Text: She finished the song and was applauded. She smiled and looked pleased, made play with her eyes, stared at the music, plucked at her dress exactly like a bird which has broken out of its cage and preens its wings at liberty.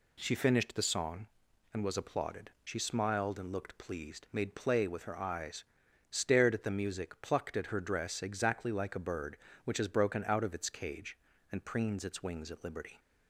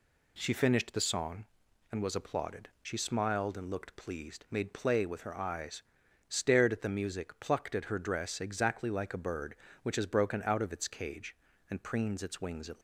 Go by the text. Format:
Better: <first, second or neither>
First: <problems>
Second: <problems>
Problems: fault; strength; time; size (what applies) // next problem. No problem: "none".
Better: first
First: none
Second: stops before "liberty"; at 12.7 s